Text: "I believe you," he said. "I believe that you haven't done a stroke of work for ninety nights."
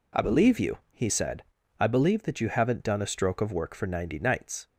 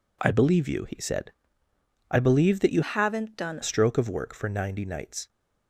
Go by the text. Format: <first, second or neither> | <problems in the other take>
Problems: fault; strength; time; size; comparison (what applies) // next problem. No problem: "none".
first | changes voice from "haven't" to "done"; from 2.8 to 3.6 s; 0.8 s long